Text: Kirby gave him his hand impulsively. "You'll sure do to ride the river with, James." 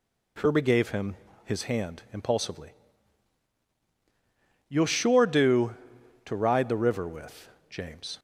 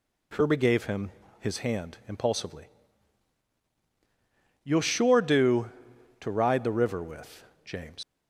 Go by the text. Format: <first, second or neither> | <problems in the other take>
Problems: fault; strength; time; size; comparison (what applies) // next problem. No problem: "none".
first | pauses between "him" and "his"; slight; at 1.1 s; 0.30 s long; slight in the first // leaves "James" unfinished; at 8.0 s; 110 ms